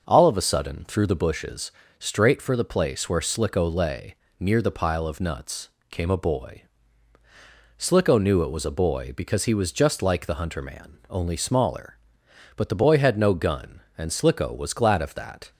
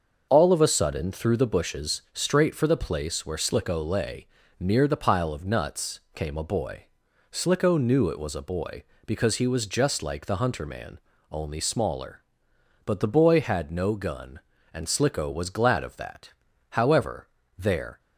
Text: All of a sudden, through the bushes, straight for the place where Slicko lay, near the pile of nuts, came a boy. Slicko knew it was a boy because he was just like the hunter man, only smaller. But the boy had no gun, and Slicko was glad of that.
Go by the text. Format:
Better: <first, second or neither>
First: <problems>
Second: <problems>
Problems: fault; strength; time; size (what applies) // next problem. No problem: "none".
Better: first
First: none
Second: starts louder than the rest; until 1.3 s; 6.5 dB // goes on to say "However there"; noticeable; from 16.7 s on; 1.2 s long